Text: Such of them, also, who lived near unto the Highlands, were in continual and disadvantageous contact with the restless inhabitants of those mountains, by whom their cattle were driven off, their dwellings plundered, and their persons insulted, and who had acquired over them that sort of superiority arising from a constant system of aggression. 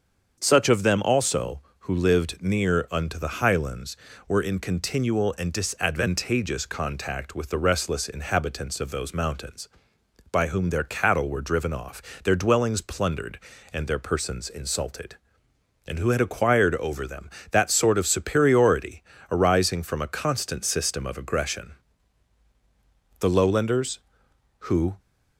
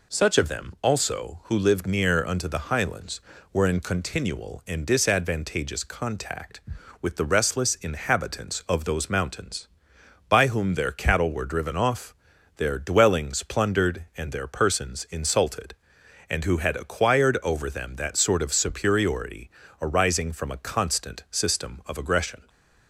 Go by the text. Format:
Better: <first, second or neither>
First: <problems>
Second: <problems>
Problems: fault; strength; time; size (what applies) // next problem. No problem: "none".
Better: second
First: starts louder than the rest; until 1.4 s; 7 dB // pauses between "superiority" and "arising"; slight; at 19.0 s; 0.28 s long // goes on to say "The Lowlanders who"; strong; from 23.1 s on; 1.8 s long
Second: pauses between "superiority" and "arising"; slight; at 19.5 s; 0.32 s long